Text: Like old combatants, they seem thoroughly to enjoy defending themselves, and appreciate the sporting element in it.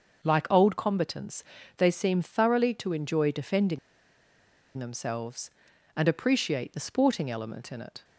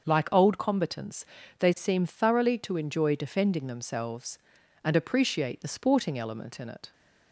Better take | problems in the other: second | starts louder than the rest; until 1.3 s; 6 dB; also in the second // pauses between "defending" and "themselves"; at 3.7 s; 0.99 s long

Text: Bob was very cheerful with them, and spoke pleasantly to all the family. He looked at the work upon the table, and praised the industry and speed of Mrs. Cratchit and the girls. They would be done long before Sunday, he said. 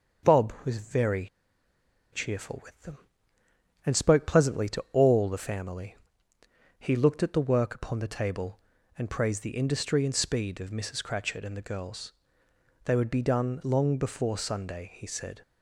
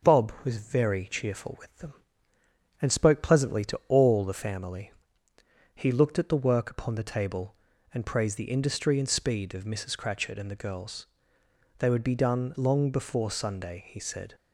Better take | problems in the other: second | starts louder than the rest; until 2.1 s; 6.5 dB; also in the second // pauses between "very" and "cheerful"; noticeable; at 1.2 s; 0.86 s long

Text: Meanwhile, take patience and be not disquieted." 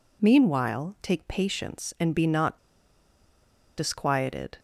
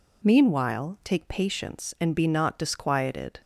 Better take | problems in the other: second | pauses between "not" and "disquieted"; at 2.5 s; 1.1 s long

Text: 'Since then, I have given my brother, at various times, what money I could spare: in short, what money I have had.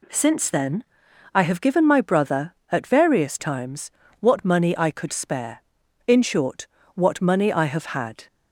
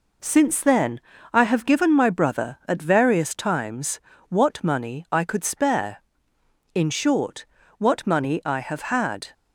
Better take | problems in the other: neither | none

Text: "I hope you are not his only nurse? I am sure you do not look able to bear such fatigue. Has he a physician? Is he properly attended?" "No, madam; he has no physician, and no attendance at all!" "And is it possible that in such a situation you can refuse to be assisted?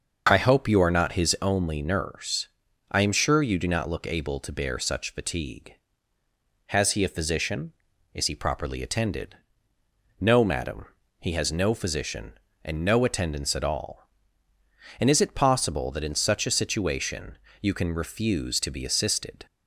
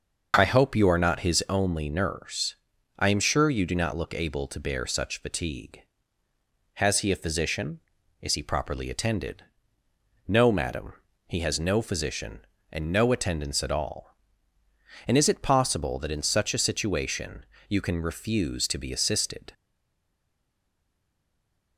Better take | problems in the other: first | starts louder than the rest; noticeable; until 1.3 s; 6 dB; also in the first // pauses between "situation" and "you"; slight; at 17.4 s; 0.24 s long; slight in the first // stays silent after the last word; from 19.5 s on; 2.2 s long

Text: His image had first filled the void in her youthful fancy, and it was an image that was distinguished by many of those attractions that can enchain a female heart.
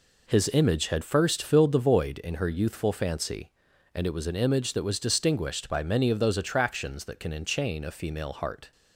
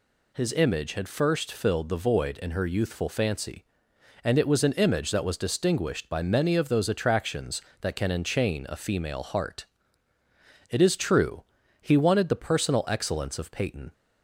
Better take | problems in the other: first | goes on to say "It is true he wanted the personal excellence of Peyton"; strong; from 10.7 s on; 3.2 s long

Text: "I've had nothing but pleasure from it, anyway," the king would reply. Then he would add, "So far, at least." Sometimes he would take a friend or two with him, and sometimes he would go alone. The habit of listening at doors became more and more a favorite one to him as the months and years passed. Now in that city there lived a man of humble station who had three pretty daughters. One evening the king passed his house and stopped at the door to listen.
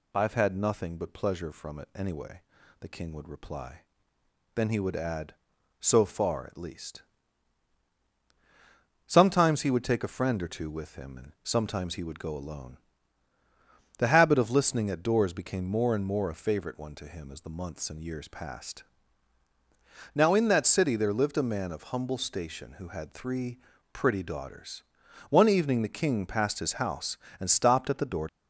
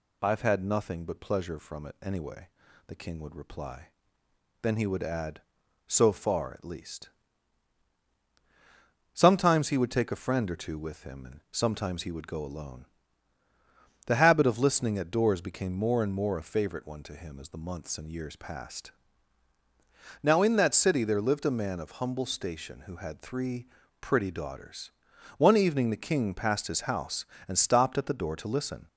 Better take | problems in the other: second | pauses between "three" and "pretty"; slight; at 23.5 s; 0.34 s long; slight in the second // stops before "to listen"; at 28.2 s

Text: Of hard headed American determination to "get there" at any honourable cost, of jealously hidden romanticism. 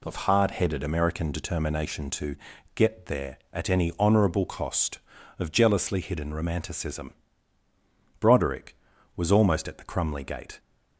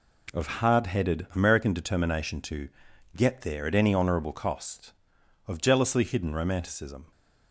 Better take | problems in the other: second | pauses between "to" and "get"; at 2.3 s; 0.40 s long; noticeable in the second // goes on to say "Broderick was almost at the Crumley gate"; strong; from 8.1 s on; 2.4 s long

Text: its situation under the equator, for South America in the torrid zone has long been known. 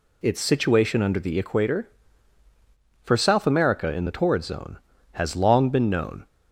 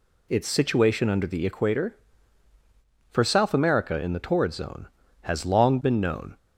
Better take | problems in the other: neither | none

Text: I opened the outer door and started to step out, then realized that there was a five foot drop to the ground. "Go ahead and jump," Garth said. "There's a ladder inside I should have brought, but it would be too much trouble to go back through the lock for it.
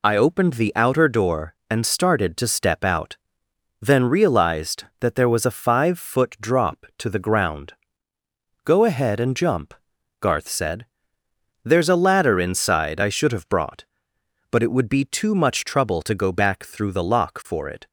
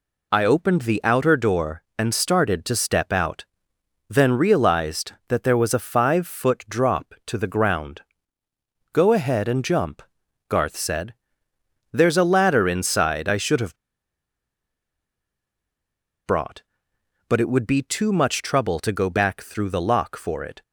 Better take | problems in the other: first | pauses between "have" and "brought"; strong; at 13.7 s; 2.4 s long

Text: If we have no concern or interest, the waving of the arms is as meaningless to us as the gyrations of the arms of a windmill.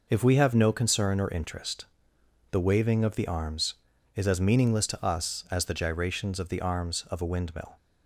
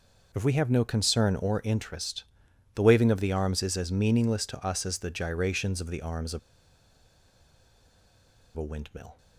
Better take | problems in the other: first | pauses between "of" and "a"; strong; at 6.3 s; 2.1 s long

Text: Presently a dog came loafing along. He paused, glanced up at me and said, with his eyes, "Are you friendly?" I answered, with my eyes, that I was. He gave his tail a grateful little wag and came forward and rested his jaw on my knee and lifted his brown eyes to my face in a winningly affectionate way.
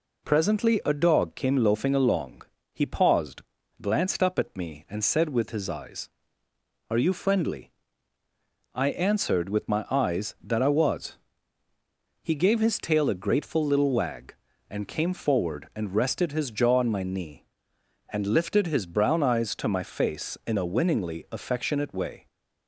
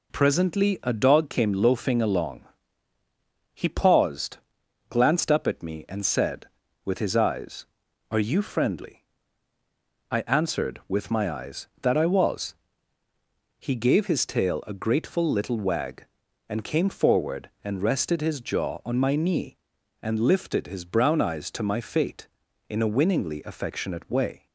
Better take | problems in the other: first | says "fate" for "face"; at 21.8 s

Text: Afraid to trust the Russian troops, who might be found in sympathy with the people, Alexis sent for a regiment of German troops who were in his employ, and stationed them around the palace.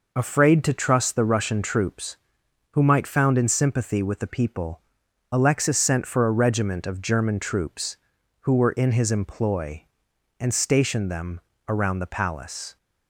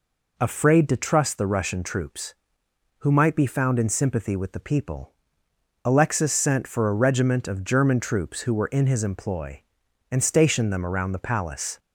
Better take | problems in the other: second | skips "be"; at 3.0 s // pauses between "them" and "around"; slight; at 11.4 s; 0.26 s long

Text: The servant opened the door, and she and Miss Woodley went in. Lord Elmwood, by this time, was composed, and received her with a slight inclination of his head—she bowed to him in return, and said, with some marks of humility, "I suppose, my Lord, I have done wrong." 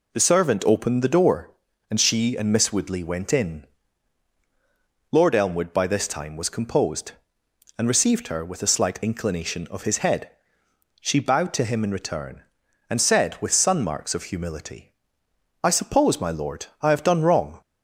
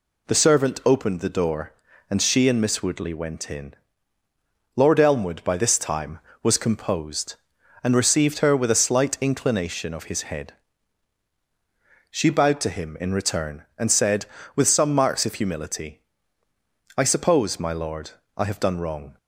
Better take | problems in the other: second | says "sun" for "some"; at 13.5 s

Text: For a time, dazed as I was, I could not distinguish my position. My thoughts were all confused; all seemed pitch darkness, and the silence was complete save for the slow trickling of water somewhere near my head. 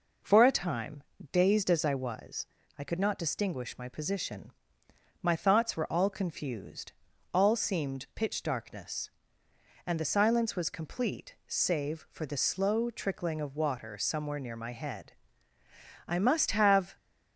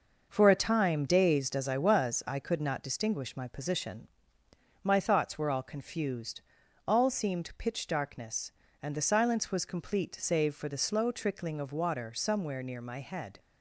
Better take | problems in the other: second | goes on to say "I must have"; noticeable; from 16.0 s on; 0.88 s long

